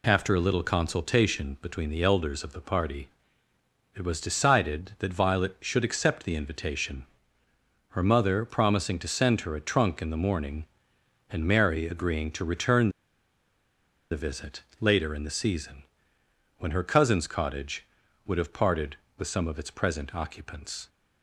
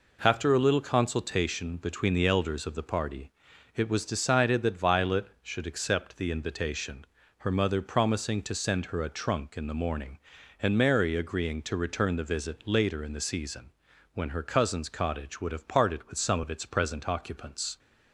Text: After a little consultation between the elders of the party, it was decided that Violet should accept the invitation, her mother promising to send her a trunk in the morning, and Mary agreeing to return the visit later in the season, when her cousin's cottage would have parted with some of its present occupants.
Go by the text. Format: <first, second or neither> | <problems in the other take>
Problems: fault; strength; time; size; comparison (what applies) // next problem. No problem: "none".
second | pauses between "return" and "the"; at 12.8 s; 1.2 s long // pauses between "visit" and "later"; slight; at 14.6 s; 0.20 s long